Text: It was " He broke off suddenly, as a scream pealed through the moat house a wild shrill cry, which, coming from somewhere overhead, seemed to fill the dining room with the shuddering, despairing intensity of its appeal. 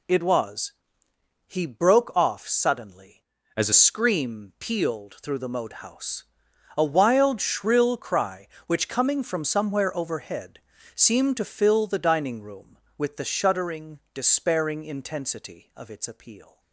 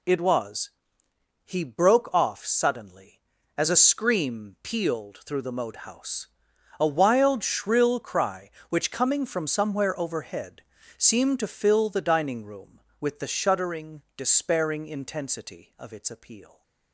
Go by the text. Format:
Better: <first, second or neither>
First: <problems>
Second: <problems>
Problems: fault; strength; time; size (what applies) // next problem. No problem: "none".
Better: second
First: changes voice from "as" to "a"; from 3.5 to 3.7 s; 0.2 s long // pauses between "house" and "a"; noticeable; at 6.2 s; 0.56 s long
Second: pauses between "house" and "a"; noticeable; at 6.2 s; 0.55 s long